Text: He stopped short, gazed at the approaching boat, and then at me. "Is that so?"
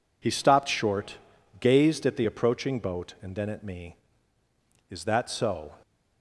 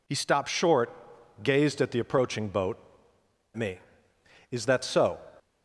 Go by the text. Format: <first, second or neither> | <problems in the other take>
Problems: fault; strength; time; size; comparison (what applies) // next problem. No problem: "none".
first | skips "and then at"; at 3.1 s